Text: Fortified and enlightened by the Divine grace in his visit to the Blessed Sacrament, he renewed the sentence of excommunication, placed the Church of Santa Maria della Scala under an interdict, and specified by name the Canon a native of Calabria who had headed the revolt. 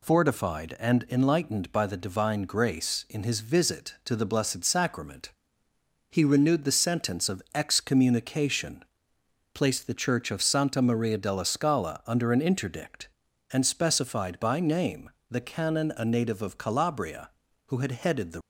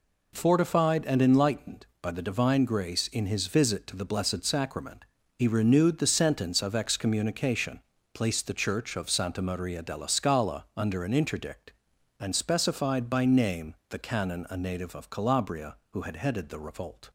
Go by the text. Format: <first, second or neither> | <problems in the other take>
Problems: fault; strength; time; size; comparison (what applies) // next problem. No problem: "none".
second | pauses between "name" and "the"; slight; at 15.0 s; 0.22 s long; slight in the second // stops before "revolt"; at 18.4 s